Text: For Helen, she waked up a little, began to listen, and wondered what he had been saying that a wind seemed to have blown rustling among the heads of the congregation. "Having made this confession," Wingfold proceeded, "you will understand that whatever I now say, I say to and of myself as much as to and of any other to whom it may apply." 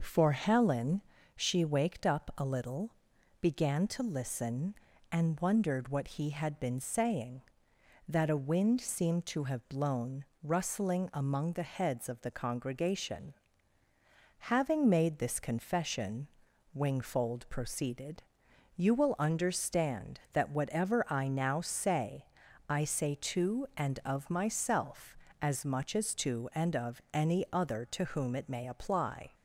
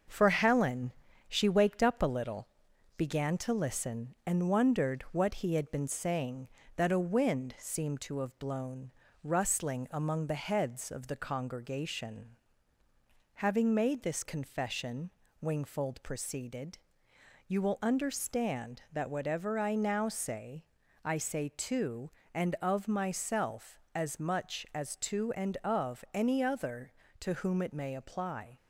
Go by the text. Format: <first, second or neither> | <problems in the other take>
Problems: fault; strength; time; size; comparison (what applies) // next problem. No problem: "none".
first | gets quieter; slight; throughout; 2.5 dB // pauses between "blown" and "rustling"; slight; at 8.9 s; 0.30 s long; slight in the first